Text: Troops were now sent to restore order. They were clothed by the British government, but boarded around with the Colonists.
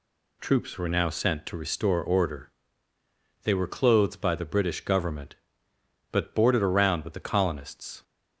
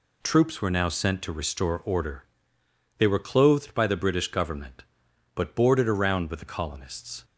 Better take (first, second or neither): neither